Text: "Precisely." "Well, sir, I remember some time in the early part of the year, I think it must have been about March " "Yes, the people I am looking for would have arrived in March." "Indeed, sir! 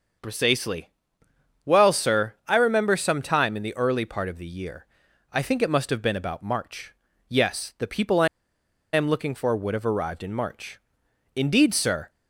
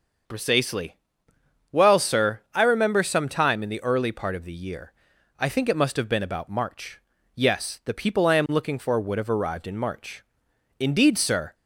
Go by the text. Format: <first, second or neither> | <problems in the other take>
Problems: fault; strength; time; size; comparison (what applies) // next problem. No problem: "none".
second | starts louder than the rest; until 1.9 s; 6.5 dB; also in the second // pauses between "I" and "am"; noticeable; at 8.2 s; 0.66 s long